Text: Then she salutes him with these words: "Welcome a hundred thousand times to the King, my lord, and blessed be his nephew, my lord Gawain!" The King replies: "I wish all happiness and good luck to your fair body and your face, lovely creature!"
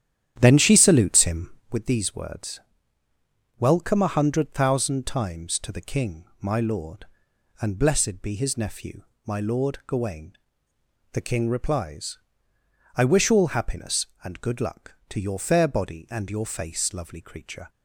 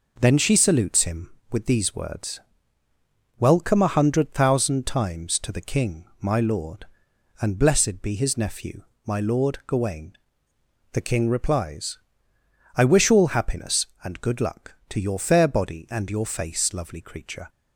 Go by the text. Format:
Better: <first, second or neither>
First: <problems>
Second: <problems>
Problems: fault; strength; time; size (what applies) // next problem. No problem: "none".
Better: second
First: starts louder than the rest; strong; until 1.8 s; 10.5 dB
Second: none